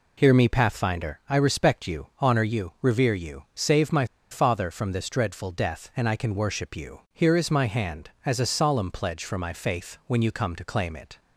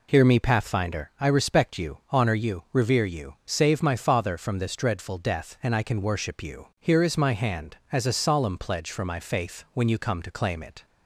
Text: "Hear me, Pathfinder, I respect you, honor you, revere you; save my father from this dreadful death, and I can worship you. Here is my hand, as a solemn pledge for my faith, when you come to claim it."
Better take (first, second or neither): second